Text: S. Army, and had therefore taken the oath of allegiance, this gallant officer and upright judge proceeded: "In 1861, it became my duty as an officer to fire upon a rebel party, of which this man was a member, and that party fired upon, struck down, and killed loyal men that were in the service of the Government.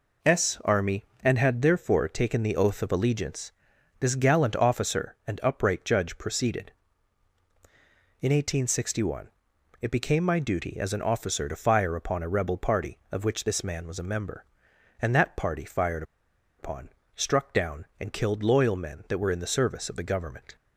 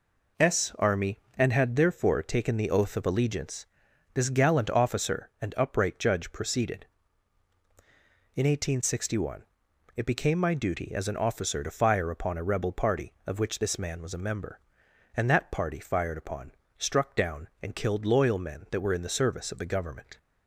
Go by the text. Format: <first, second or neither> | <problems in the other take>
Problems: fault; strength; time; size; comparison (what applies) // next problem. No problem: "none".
second | pauses between "fired" and "upon"; noticeable; at 16.0 s; 0.55 s long